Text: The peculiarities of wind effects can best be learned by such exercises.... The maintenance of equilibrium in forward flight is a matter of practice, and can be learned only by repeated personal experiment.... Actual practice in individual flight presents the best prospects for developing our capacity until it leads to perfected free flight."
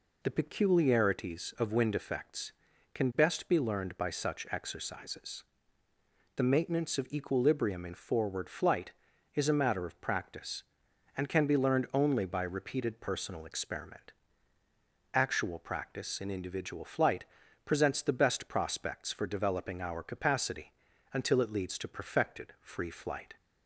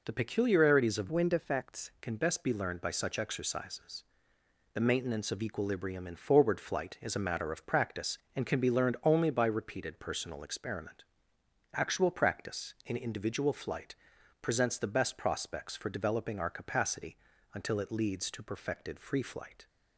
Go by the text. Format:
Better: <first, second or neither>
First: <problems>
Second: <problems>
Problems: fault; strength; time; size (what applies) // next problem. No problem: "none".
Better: first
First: pauses between "flight" and "presents"; at 17.2 s; 0.40 s long // pauses between "capacity" and "until"; at 20.7 s; 0.40 s long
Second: changes voice from "wind" to "effects"; from 1.1 to 1.9 s; 0.8 s long // pauses between "flight" and "presents"; at 13.9 s; 0.44 s long // pauses between "capacity" and "until"; slight; at 17.1 s; 0.36 s long